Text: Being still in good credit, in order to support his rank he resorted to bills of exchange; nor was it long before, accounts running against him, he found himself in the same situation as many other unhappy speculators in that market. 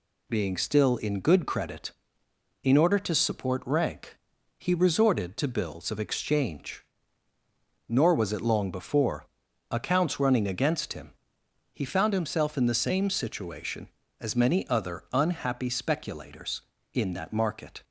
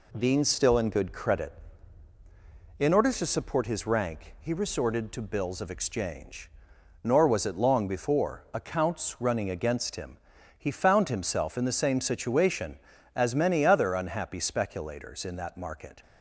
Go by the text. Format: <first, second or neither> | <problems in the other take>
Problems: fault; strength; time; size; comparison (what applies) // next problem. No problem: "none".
second | skips "his"; at 3.6 s // pauses between "rank" and "he"; at 4.1 s; 0.40 s long